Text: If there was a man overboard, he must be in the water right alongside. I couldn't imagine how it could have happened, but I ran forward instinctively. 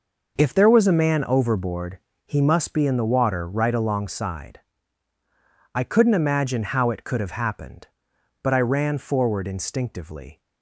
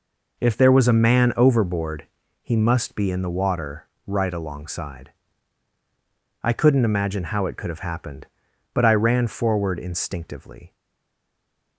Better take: first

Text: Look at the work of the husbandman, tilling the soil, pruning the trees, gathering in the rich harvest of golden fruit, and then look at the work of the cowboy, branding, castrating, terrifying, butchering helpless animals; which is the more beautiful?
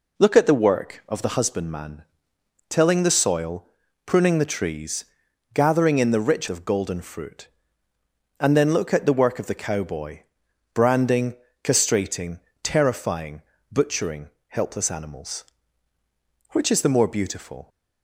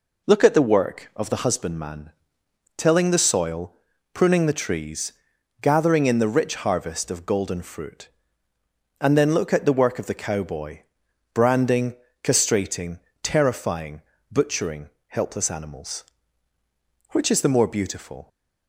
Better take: second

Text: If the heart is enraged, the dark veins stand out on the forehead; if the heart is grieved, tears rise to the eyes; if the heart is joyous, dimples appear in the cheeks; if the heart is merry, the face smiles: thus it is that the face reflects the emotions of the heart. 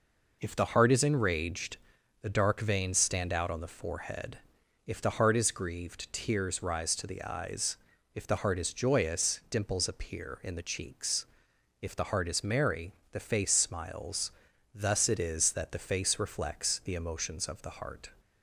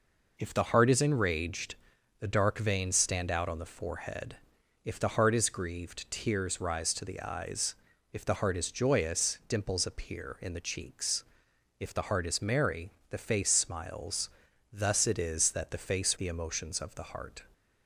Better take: first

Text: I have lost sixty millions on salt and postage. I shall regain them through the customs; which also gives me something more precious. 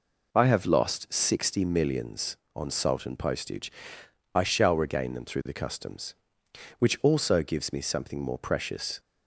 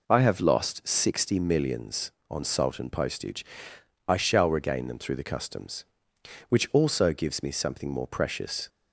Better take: neither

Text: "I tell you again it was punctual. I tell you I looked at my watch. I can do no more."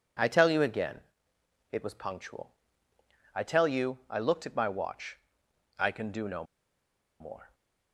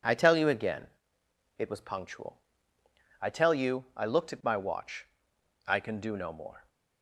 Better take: second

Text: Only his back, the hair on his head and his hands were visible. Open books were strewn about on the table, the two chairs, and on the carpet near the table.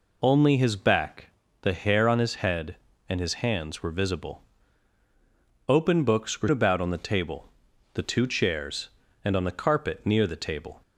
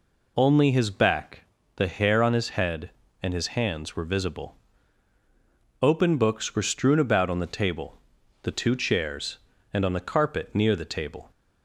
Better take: second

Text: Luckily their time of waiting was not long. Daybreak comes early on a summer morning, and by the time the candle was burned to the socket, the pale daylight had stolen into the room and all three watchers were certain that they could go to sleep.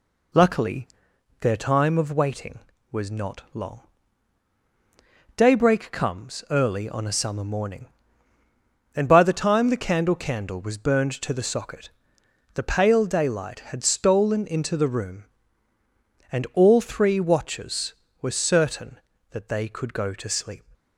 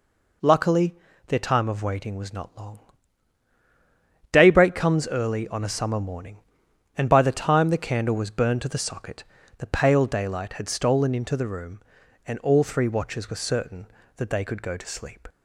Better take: second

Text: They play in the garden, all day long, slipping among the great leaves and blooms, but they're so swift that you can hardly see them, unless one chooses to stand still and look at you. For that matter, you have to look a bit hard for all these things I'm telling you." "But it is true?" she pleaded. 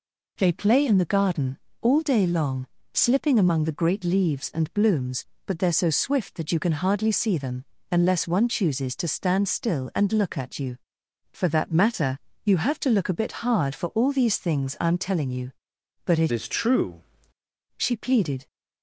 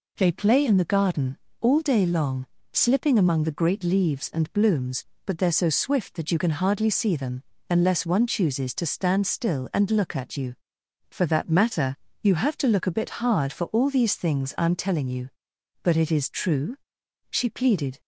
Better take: second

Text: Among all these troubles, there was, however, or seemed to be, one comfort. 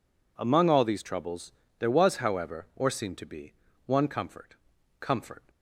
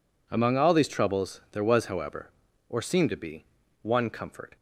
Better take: second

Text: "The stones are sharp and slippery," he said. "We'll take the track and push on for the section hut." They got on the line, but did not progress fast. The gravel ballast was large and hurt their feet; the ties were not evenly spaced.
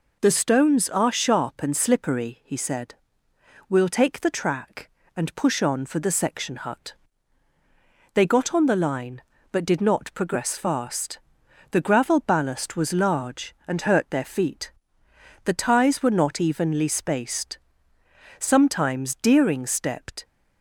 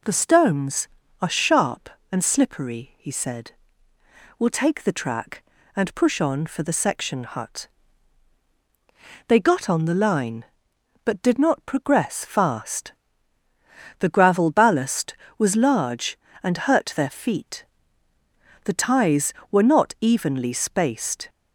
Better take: second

